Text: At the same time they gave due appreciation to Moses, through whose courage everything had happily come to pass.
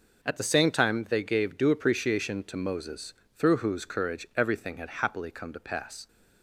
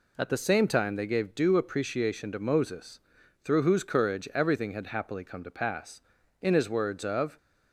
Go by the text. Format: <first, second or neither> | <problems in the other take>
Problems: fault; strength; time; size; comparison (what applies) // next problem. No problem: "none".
first | goes on to say "In his words of"; noticeable; from 6.4 s on; 0.96 s long